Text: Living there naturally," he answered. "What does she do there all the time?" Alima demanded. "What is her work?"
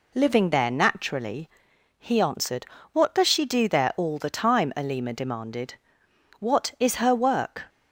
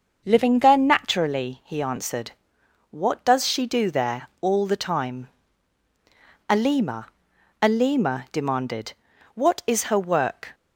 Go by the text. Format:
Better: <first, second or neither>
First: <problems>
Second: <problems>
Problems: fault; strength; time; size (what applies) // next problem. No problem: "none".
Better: first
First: none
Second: starts louder than the rest; until 1.2 s; 6 dB // says "Alima" twice; at 7.6 s